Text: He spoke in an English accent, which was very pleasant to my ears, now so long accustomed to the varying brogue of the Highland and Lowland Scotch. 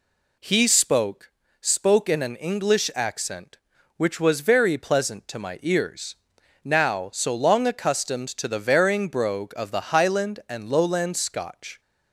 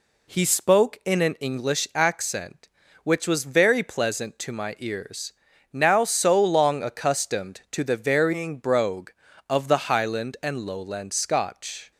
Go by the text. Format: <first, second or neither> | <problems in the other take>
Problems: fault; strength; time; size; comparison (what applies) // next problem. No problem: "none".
second | says "spoke" twice; at 1.5 s